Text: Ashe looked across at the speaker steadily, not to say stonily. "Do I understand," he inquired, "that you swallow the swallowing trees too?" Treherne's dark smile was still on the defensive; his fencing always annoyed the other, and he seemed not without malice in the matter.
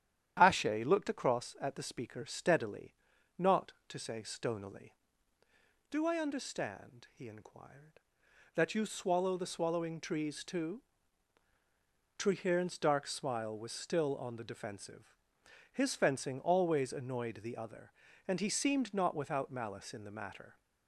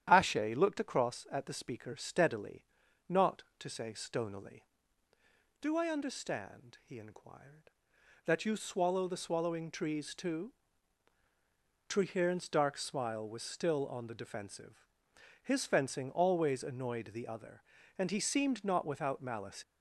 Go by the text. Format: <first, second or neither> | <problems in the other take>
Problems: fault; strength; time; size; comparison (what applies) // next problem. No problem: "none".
first | starts louder than the rest; strong; until 1.0 s; 10.5 dB; strong in the first // stops before "in the matter"; at 19.6 s